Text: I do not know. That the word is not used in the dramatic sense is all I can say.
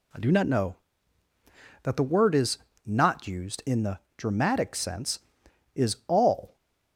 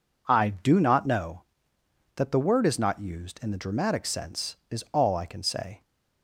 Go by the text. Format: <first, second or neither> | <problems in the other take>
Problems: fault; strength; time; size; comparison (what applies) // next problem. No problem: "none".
second | pauses between "is" and "not"; slight; at 2.5 s; 0.26 s long // pauses between "the" and "dramatic"; slight; at 3.9 s; 0.18 s long // stops before "I can say"; at 6.5 s